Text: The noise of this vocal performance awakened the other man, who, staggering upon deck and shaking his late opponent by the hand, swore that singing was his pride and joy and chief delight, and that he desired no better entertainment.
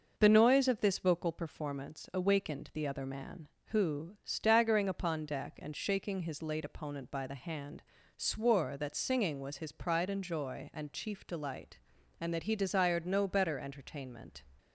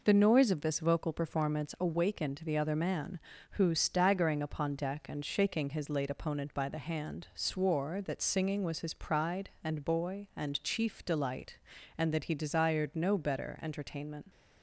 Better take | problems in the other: first | says "boy" for "joy"; at 9.8 s

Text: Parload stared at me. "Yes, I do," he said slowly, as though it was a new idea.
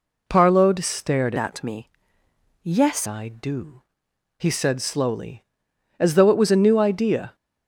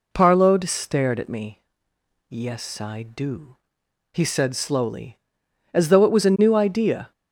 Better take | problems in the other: second | changes voice from "at" to "Yes"; from 1.3 to 3.0 s; 1.7 s long

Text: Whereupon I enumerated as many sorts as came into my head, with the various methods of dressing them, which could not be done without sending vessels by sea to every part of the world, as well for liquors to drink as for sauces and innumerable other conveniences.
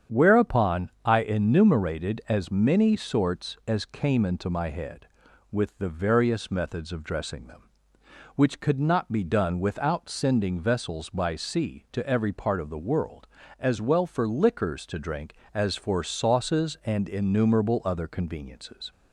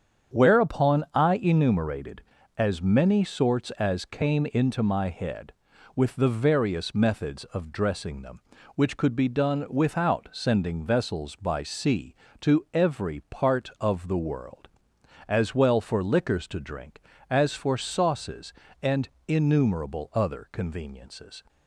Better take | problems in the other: first | starts louder than the rest; strong; until 1.4 s; 8 dB; strong in the first // skips "not"; at 9.1 s // pauses between "and" and "innumerable"; slight; at 19.0 s; 0.18 s long

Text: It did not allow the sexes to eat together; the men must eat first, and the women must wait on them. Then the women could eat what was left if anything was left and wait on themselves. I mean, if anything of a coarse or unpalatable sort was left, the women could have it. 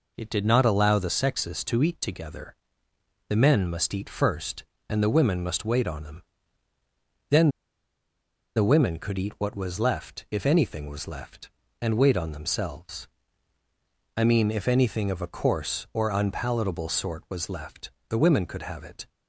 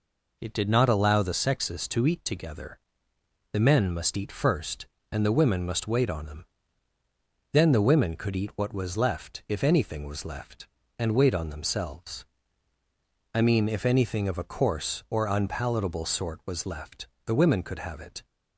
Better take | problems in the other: second | pauses between "Then" and "the"; at 7.4 s; 1.0 s long

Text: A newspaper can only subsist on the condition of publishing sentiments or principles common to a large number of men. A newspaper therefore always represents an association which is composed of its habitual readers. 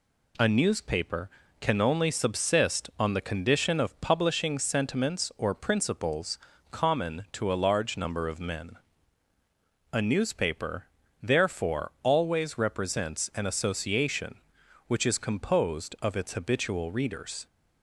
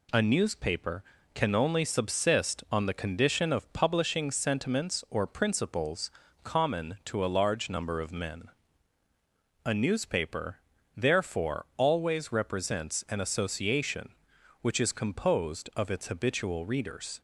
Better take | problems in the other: neither | pauses between "principles" and "common"; slight; the same in both // pauses between "newspaper" and "therefore"; slight; the same in both

